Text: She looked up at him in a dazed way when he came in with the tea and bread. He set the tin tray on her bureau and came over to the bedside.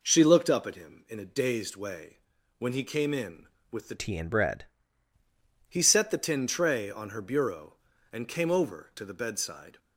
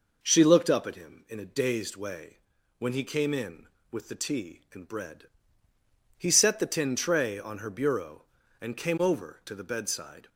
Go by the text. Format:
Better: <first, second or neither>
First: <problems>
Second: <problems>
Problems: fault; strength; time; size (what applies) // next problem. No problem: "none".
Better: second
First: pauses between "way" and "when"; at 2.1 s; 0.40 s long // changes voice from "tea" to "bread"; from 3.9 to 4.6 s; 0.7 s long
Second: pauses between "way" and "when"; at 2.3 s; 0.40 s long